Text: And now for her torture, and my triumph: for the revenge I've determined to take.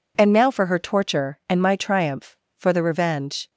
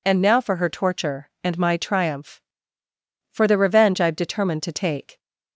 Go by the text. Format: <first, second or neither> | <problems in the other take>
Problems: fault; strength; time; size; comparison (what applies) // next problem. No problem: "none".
second | stops before "I've determined to take"; at 3.4 s